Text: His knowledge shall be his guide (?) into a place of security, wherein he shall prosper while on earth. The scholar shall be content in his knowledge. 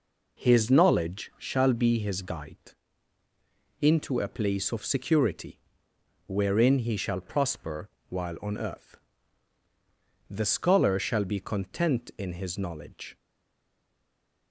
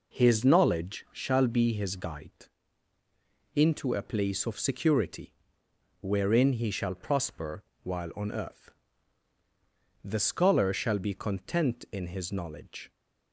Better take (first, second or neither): second